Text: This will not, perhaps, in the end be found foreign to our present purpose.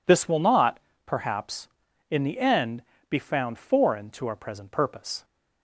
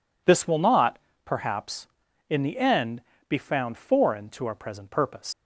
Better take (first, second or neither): first